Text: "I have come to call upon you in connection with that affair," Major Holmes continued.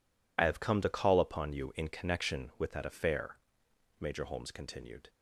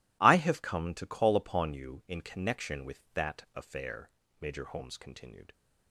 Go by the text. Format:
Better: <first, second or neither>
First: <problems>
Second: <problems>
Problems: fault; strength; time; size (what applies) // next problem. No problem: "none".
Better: second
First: loses the start of "I"; at 0.3 s; 30 ms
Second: none